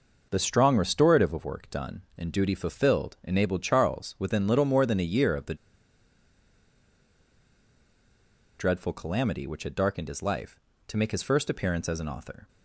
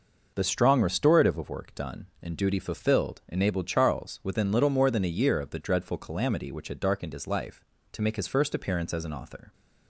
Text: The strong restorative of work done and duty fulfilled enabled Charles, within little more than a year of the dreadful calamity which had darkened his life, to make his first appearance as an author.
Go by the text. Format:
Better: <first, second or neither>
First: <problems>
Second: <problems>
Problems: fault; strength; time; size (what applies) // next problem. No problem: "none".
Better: second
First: pauses between "the" and "dreadful"; strong; at 5.5 s; 3.0 s long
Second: none